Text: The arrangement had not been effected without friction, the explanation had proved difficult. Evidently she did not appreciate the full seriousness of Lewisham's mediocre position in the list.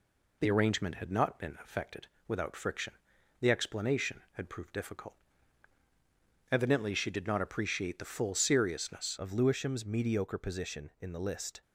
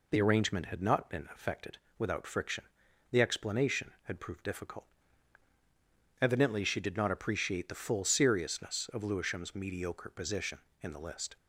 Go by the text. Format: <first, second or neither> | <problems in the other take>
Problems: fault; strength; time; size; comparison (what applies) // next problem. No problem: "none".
second | pauses between "effected" and "without"; slight; at 2.0 s; 0.20 s long; slight in the second // changes voice at "of"; from 9.1 s on; 2.5 s long